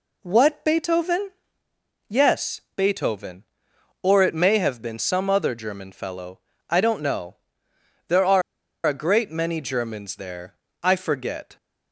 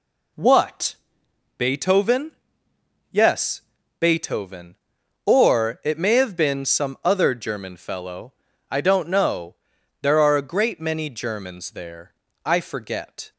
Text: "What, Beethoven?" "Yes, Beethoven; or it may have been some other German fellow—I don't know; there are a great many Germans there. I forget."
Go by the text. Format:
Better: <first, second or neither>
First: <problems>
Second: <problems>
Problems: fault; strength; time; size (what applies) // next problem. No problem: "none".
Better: second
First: pauses between "are" and "a"; at 8.4 s; 0.44 s long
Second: none